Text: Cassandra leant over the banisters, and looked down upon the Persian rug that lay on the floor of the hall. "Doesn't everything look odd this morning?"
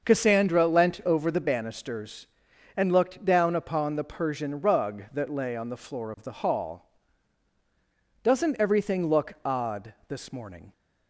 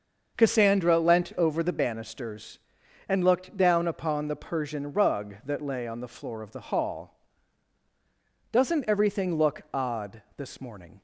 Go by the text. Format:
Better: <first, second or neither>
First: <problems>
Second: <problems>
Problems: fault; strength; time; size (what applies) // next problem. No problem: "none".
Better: neither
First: starts louder than the rest; until 1.1 s; 6.5 dB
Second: starts louder than the rest; until 1.4 s; 6.5 dB